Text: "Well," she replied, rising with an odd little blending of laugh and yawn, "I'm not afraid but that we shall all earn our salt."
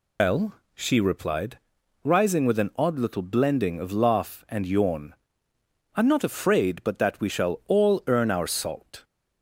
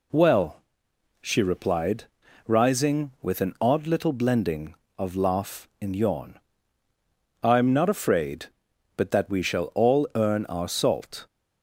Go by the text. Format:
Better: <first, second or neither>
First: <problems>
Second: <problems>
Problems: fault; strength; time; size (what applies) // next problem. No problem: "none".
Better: second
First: loses the start of "Well"; at 0.1 s; 135 ms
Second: none